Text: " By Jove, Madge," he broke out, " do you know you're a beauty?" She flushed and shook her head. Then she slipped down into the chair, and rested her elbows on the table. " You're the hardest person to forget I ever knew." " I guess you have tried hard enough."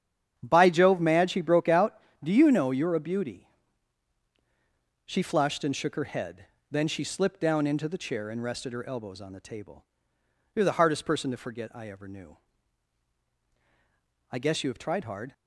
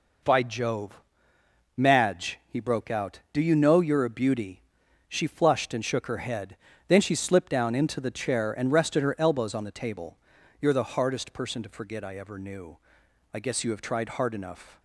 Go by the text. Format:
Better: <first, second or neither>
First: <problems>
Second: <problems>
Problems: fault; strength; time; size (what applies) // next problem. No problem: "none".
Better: second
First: starts louder than the rest; strong; until 1.3 s; 10.5 dB // stops before "enough"; at 15.3 s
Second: none